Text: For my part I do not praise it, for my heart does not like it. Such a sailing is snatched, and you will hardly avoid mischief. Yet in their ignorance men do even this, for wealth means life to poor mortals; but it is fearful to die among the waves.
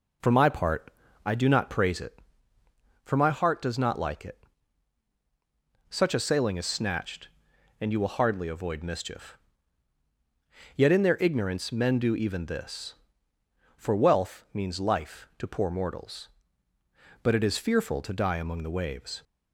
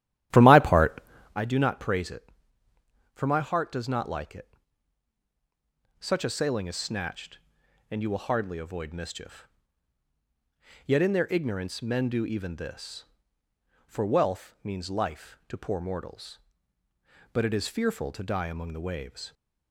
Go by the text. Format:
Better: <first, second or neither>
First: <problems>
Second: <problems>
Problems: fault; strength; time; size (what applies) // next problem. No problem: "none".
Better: first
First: pauses between "part" and "I"; slight; at 0.9 s; 0.34 s long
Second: starts louder than the rest; strong; until 1.4 s; 13 dB // pauses between "part" and "I"; slight; at 1.0 s; 0.34 s long